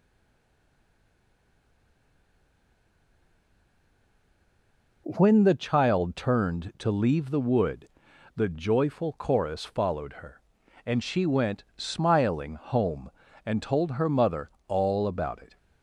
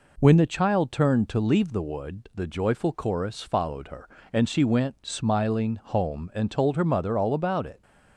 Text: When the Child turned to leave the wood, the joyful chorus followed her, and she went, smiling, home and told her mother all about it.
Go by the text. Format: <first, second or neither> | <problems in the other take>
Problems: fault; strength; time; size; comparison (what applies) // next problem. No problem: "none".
second | stays silent before the first word; strong; until 5.0 s; 5.0 s long // pauses between "mother" and "all"; slight; at 14.4 s; 0.18 s long